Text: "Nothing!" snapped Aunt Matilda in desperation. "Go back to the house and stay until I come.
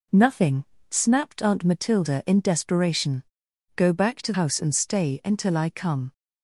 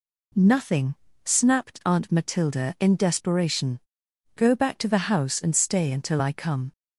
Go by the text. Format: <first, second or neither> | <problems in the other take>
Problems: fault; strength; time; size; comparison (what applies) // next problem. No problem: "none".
second | skips "the"; at 4.3 s